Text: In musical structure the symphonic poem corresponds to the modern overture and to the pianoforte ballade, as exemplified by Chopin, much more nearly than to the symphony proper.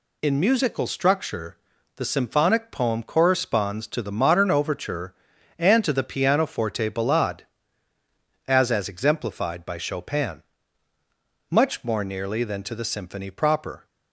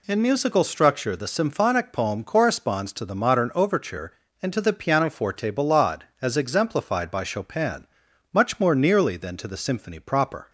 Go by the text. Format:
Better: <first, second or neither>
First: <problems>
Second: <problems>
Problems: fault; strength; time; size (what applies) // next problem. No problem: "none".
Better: second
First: pauses between "structure" and "the"; at 1.5 s; 0.40 s long // says "as" twice; at 8.6 s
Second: none